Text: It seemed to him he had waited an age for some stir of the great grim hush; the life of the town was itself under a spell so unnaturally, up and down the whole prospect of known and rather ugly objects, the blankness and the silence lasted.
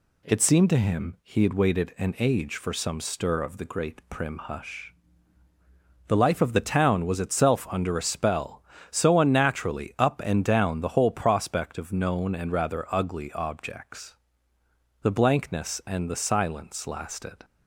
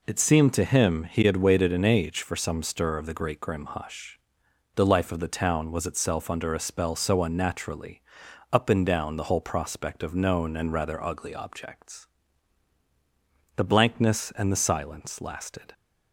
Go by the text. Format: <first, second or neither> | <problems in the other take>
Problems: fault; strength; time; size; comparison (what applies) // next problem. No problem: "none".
second | says "prim" for "grim"; at 4.0 s